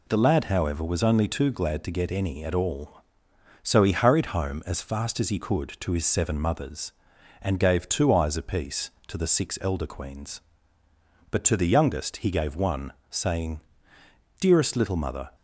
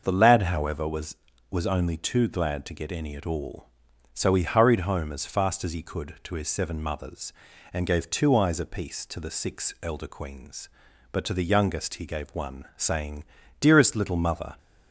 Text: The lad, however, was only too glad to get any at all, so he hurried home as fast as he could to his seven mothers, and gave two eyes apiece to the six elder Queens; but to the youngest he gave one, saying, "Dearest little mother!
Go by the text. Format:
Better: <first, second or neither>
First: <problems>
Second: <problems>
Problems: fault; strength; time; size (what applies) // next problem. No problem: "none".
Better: first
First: none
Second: starts louder than the rest; noticeable; until 1.0 s; 6 dB // says "was" twice; at 1.5 s